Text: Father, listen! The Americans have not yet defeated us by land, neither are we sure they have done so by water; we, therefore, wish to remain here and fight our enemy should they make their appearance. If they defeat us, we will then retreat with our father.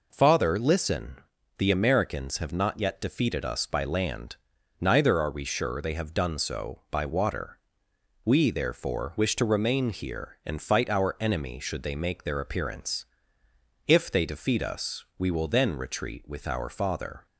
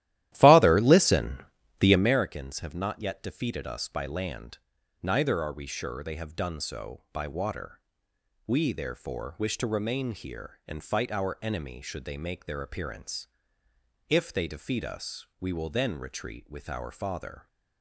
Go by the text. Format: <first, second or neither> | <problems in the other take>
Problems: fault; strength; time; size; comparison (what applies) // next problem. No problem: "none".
first | starts louder than the rest; strong; until 2.2 s; 14 dB